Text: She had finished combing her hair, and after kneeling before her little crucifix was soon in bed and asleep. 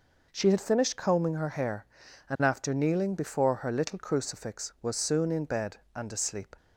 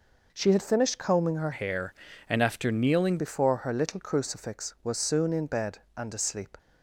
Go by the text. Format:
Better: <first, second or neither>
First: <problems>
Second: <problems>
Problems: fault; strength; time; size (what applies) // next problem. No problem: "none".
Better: first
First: none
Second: changes voice from "hair" to "kneeling"; from 1.5 to 3.1 s; 1.6 s long